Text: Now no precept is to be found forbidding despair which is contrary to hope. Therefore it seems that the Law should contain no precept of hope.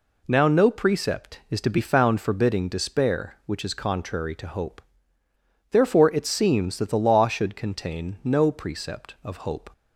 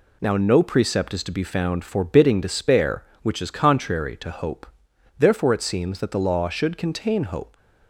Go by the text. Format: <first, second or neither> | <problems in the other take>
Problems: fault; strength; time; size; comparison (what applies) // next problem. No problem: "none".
first | skips "no precept of"; at 7.2 s